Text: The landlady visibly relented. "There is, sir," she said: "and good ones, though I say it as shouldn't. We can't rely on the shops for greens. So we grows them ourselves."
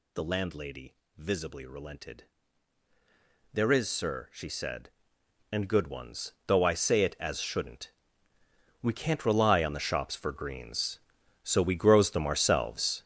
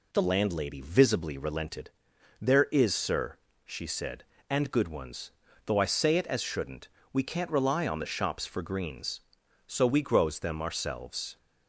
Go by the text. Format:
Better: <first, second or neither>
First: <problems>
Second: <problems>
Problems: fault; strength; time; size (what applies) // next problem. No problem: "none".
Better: second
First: gets louder; strong; throughout; 10 dB // pauses between "landlady" and "visibly"; slight; at 0.9 s; 0.22 s long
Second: none